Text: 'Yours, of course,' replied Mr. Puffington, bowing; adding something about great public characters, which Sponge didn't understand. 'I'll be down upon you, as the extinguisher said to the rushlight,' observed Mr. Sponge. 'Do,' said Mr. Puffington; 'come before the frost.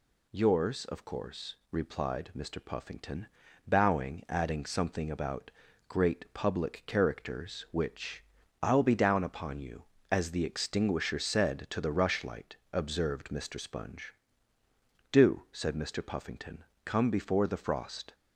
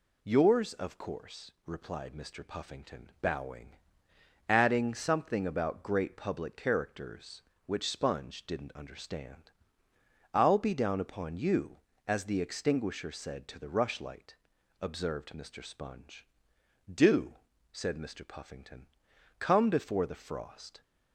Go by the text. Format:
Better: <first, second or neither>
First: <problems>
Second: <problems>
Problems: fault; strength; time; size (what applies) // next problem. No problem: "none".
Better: second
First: pauses between "about" and "great"; at 5.4 s; 0.38 s long // skips "Sponge didn't understand"; at 8.4 s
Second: none